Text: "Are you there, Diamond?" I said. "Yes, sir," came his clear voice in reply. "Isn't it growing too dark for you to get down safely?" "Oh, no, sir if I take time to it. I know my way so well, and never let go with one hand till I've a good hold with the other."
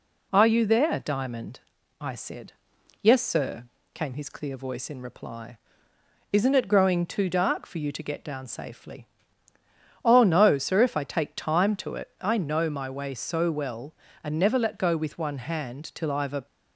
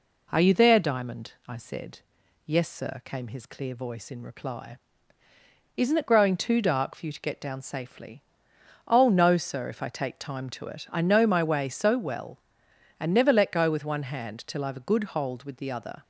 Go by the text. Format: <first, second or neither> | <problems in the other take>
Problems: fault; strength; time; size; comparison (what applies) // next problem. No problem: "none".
second | stops before "good hold with the other"; at 16.4 s